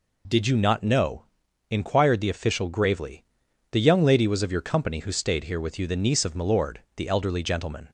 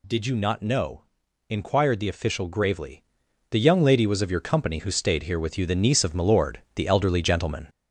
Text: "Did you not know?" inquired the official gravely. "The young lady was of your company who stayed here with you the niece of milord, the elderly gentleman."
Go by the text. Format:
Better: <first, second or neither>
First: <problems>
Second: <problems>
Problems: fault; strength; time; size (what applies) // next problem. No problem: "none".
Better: first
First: none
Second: gets louder; noticeable; throughout; 4.5 dB